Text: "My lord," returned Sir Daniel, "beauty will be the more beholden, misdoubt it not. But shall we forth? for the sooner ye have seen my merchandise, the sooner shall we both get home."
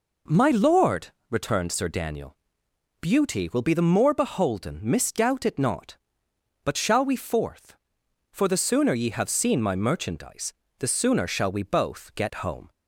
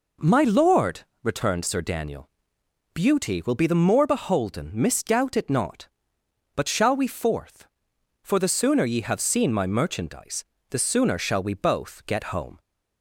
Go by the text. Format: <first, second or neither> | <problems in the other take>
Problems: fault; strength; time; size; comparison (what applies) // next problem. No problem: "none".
neither | none